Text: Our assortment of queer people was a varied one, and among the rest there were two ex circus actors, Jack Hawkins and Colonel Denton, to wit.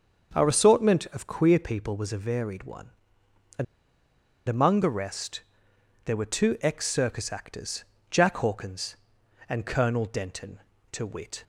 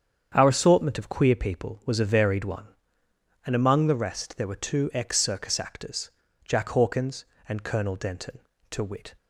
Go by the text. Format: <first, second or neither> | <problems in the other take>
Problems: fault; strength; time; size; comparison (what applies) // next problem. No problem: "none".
second | starts louder than the rest; until 1.4 s; 6.5 dB; strong in the second // pauses between "and" and "among"; noticeable; at 3.6 s; 0.84 s long // pauses between "rest" and "there"; noticeable; at 5.4 s; 0.64 s long